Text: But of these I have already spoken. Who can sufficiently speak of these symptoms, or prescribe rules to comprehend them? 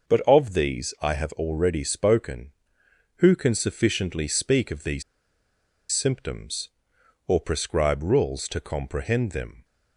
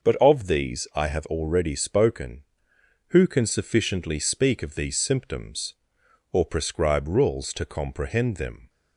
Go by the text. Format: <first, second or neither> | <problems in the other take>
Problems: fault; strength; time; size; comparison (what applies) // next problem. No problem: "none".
second | starts louder than the rest; noticeable; until 1.2 s; 6 dB // pauses between "these" and "symptoms"; noticeable; at 5.0 s; 0.89 s long